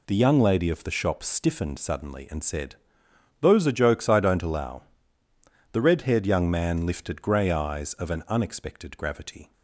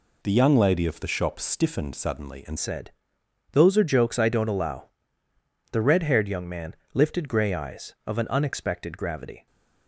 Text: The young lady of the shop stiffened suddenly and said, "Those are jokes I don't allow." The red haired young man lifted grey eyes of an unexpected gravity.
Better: first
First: none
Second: changes voice at "said"; from 2.5 s on; 6.9 s long // pauses between "man" and "lifted"; slight; at 6.7 s; 0.18 s long

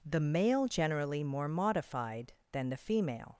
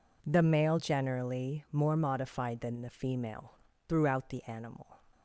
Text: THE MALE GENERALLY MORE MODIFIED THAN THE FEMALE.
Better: first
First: none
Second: goes on to say "Throughout the animal"; noticeable; from 3.8 s on; 1.1 s long

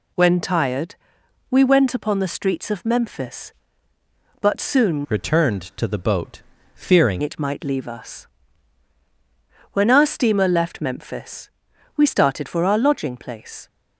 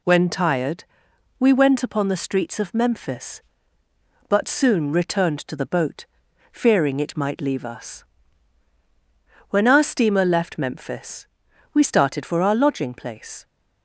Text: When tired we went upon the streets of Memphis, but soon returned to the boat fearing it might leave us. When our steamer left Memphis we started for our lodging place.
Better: second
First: pauses between "tired" and "we"; noticeable; at 0.9 s; 0.56 s long // changes voice from "returned" to "fearing"; from 5.0 to 7.2 s; 2.2 s long // pauses between "boat" and "fearing"; slight; at 6.3 s; 0.36 s long // pauses between "Memphis" and "we"; noticeable; at 11.4 s; 0.48 s long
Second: pauses between "tired" and "we"; noticeable; at 0.8 s; 0.56 s long // pauses between "boat" and "fearing"; noticeable; at 6.0 s; 0.46 s long // pauses between "Memphis" and "we"; noticeable; at 11.2 s; 0.48 s long

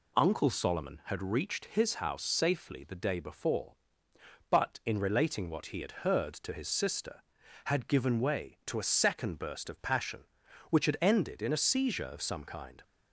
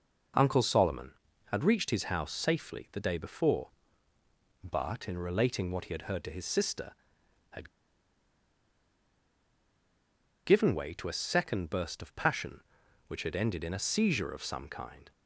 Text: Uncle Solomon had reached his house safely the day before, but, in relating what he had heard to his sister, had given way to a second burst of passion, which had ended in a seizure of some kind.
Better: first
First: none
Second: pauses between "had" and "given"; strong; at 7.6 s; 2.7 s long

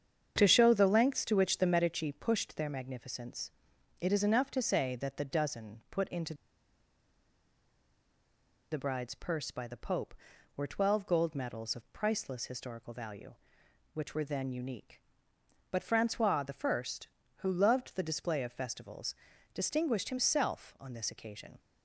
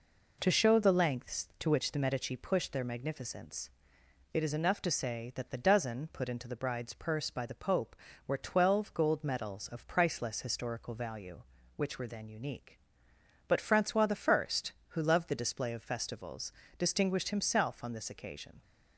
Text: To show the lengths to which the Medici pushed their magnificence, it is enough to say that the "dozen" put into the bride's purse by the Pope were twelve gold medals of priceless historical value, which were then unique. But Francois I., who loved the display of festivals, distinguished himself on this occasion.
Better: second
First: starts louder than the rest; strong; until 1.3 s; 7.5 dB // pauses between "into" and "the"; strong; at 6.3 s; 2.3 s long // pauses between "Francois" and "I"; slight; at 16.4 s; 0.20 s long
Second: none

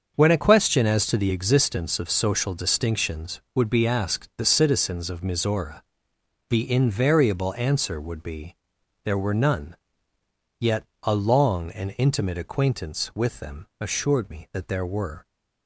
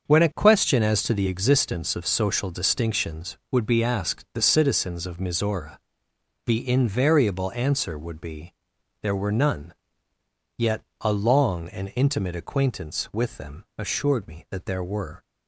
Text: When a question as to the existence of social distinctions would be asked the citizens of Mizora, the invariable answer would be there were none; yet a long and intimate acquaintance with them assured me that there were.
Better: neither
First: starts louder than the rest; until 1.1 s; 6.5 dB // pauses between "be" and "there"; noticeable; at 8.5 s; 0.48 s long // pauses between "yet" and "a"; slight; at 10.8 s; 0.20 s long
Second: starts louder than the rest; until 1.1 s; 6.5 dB // pauses between "be" and "there"; noticeable; at 8.5 s; 0.48 s long // pauses between "yet" and "a"; slight; at 10.8 s; 0.20 s long

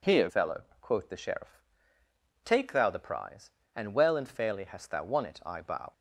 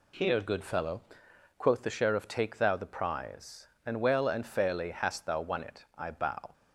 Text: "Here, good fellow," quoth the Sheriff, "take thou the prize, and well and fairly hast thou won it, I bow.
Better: second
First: skips "good"; at 0.2 s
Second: none

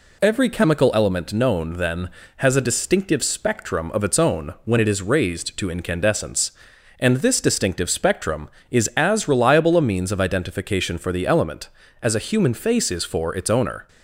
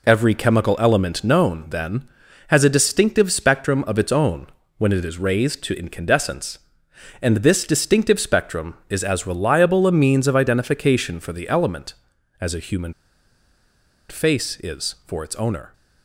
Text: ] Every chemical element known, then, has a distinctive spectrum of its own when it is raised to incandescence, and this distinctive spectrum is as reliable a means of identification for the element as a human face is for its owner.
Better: first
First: none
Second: pauses between "own" and "when"; slight; at 4.4 s; 0.30 s long // pauses between "human" and "face"; at 12.9 s; 1.1 s long

